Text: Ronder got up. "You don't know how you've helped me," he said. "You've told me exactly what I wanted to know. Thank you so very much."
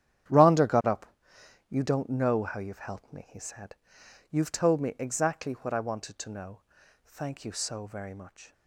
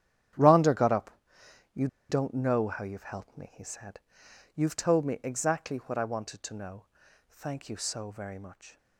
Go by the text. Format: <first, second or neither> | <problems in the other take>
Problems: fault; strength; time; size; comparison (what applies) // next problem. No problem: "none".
first | starts louder than the rest; strong; until 2.2 s; 10 dB; strong in the first // pauses between "You" and "don't"; slight; at 1.8 s; 0.22 s long